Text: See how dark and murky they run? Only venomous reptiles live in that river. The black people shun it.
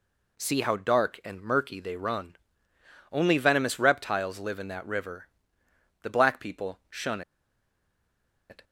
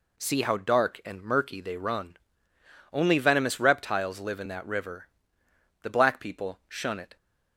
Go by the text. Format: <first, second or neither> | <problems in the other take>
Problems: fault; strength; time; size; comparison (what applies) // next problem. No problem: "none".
second | pauses between "shun" and "it"; strong; at 7.2 s; 1.2 s long